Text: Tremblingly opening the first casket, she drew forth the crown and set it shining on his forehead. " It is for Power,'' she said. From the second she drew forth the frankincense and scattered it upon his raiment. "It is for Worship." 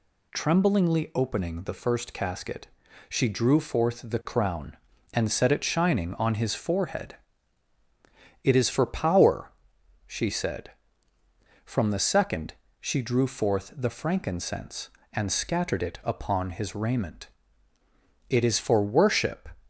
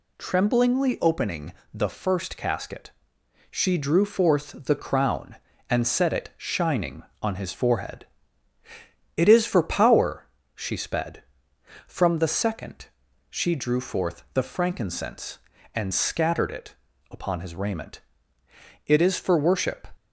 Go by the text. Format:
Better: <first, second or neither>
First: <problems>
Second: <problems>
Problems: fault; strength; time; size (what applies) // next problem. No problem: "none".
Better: first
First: pauses between "second" and "she"; slight; at 12.5 s; 0.26 s long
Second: pauses between "opening" and "the"; slight; at 1.5 s; 0.20 s long // says "sped" for "said"; at 10.7 s // pauses between "second" and "she"; at 12.8 s; 0.44 s long // pauses between "it" and "upon"; slight; at 16.7 s; 0.34 s long